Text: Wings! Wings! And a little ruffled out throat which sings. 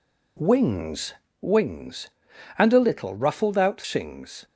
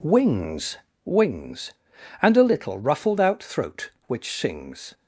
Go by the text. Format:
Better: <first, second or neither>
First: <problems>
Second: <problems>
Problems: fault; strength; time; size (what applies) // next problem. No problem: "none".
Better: second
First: skips "throat which"; at 3.8 s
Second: none